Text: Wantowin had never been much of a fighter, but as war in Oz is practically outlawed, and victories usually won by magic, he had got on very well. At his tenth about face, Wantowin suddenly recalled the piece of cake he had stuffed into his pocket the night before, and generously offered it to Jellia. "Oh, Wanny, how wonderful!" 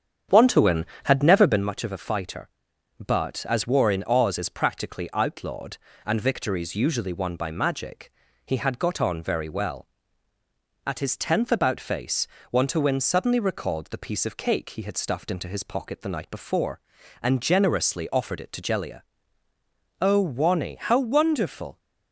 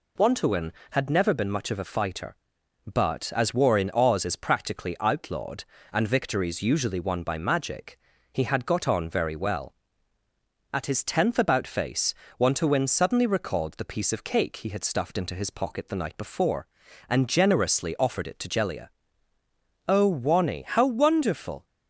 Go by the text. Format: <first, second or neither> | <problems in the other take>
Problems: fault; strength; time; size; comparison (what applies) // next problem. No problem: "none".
second | starts louder than the rest; strong; until 1.7 s; 8 dB